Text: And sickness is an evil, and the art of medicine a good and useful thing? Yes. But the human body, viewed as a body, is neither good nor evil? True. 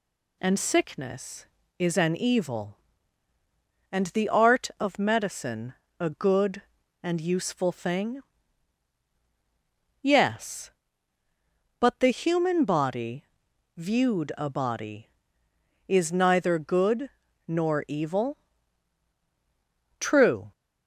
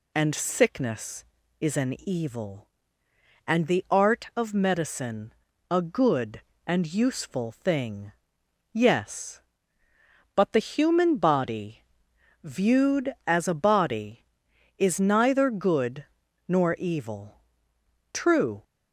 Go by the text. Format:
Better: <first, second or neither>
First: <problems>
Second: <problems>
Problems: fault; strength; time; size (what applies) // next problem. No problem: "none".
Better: second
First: pauses between "medicine" and "a"; slight; at 5.7 s; 0.26 s long // skips "as"; at 14.3 s // pauses between "good" and "nor"; at 17.0 s; 0.38 s long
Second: pauses between "medicine" and "a"; slight; at 5.3 s; 0.36 s long // pauses between "good" and "nor"; at 16.0 s; 0.42 s long